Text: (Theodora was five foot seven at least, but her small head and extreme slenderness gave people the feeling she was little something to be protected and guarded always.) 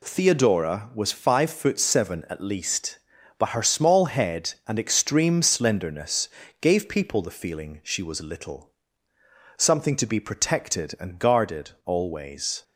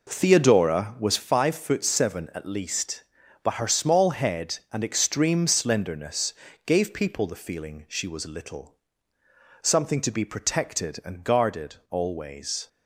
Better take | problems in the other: first | starts louder than the rest; noticeable; until 1.3 s; 4.5 dB // pauses between "slenderness" and "gave"; slight; at 6.3 s; 0.32 s long; slight in the first // pauses between "little" and "something"; noticeable; at 8.7 s; 0.84 s long; noticeable in the first

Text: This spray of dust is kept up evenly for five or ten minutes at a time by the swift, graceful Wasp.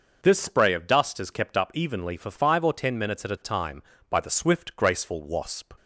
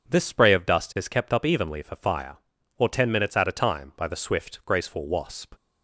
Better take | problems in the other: first | says "fire" for "five"; at 1.9 s

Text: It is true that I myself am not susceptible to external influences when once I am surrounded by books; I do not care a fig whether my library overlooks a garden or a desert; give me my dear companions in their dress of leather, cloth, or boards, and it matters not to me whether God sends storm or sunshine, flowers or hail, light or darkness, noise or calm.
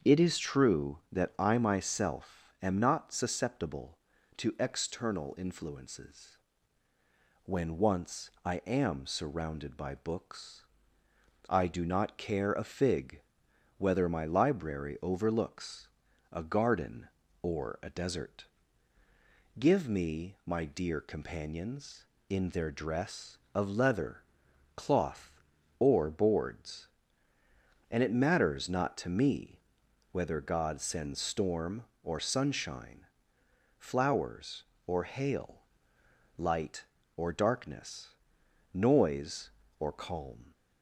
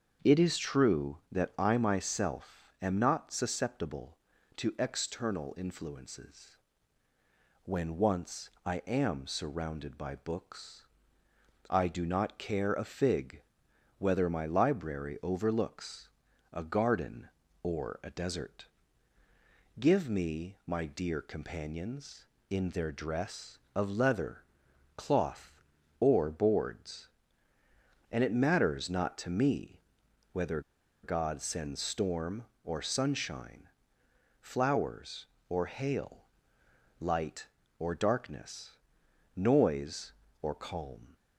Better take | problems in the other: first | starts louder than the rest; until 1.3 s; 7 dB; also in the first // pauses between "influences" and "when"; at 6.5 s; 1.0 s long; also in the first // pauses between "once" and "I"; slight; at 8.4 s; 0.16 s long // pauses between "fig" and "whether"; noticeable; at 13.4 s; 0.56 s long; noticeable in the first // pauses between "overlooks" and "a"; at 16.0 s; 0.44 s long; also in the first // pauses between "me" and "whether"; noticeable; at 29.7 s; 0.54 s long; noticeable in the first // pauses between "whether" and "God"; at 30.6 s; 0.42 s long

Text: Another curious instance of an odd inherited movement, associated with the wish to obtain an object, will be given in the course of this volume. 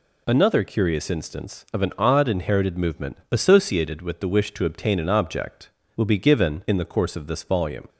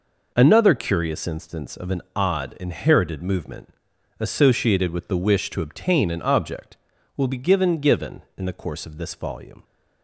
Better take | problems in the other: first | says "given" twice; at 7.7 s

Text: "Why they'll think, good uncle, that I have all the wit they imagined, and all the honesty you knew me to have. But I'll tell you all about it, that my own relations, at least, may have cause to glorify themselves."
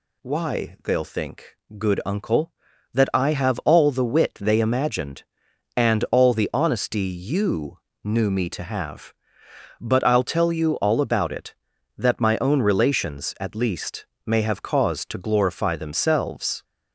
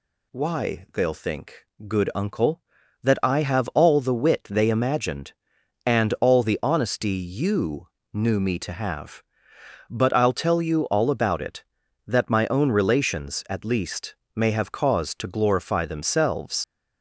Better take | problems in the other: first | pauses between "you" and "knew"; slight; at 7.8 s; 0.26 s long; slight in the first // leaves "themselves" unfinished; at 16.6 s; 90 ms

